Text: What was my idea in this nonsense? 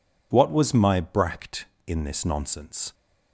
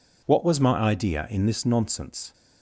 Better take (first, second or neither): second